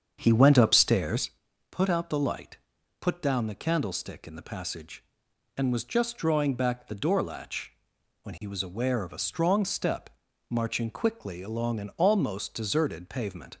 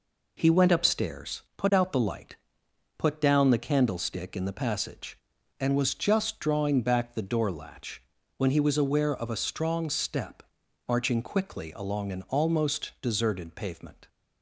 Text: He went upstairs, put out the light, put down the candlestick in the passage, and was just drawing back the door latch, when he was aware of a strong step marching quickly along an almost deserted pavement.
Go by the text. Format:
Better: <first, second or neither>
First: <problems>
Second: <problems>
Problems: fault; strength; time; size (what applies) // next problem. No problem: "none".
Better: second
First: starts louder than the rest; strong; until 1.3 s; 7.5 dB // pauses between "step" and "marching"; at 10.0 s; 0.40 s long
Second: pauses between "step" and "marching"; noticeable; at 10.4 s; 0.46 s long